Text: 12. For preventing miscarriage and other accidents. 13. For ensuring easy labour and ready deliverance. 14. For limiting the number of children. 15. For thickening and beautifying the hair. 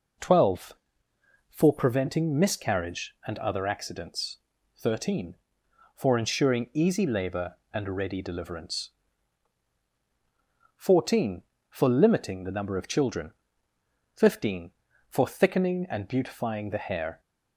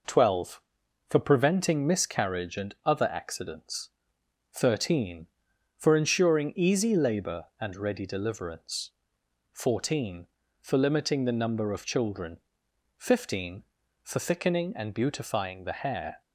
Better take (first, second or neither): neither